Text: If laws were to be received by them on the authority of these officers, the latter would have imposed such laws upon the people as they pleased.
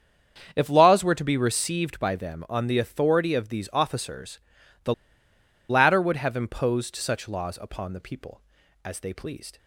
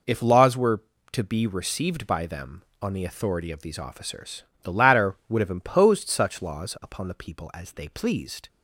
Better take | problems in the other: second | starts louder than the rest; strong; until 1.5 s; 7.5 dB // pauses between "the" and "latter"; noticeable; at 4.9 s; 0.75 s long

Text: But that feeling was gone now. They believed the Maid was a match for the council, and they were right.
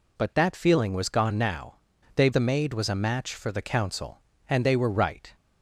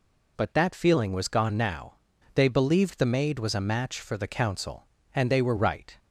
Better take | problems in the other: second | skips "believed"; at 2.3 s

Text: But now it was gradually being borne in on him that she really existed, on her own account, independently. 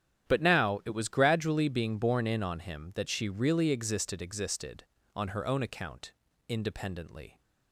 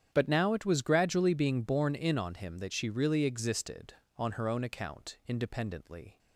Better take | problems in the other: second | starts louder than the rest; strong; until 1.3 s; 10 dB; strong in the second // says "existed" twice; at 4.1 s

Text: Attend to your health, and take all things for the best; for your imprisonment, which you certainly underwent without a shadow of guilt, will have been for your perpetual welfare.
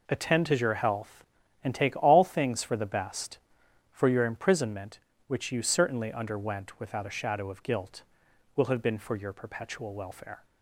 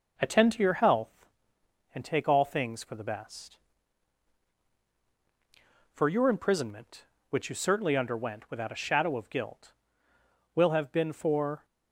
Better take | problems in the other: first | stops before "your perpetual welfare"; at 11.6 s

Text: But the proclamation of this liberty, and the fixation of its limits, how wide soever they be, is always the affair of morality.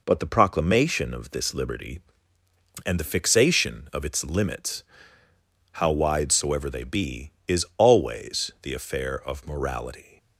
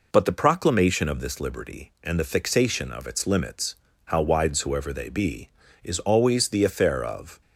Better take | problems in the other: first | stops before "morality"; at 7.4 s

